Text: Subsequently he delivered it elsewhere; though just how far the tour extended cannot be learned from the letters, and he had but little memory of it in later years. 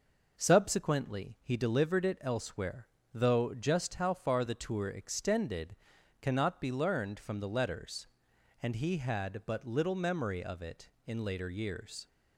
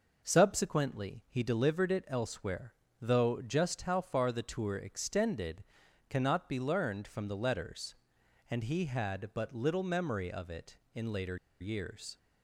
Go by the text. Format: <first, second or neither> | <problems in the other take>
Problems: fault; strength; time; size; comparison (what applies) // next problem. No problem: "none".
first | pauses between "extended" and "cannot"; at 5.6 s; 0.44 s long; also in the first // pauses between "later" and "years"; slight; at 11.3 s; 0.23 s long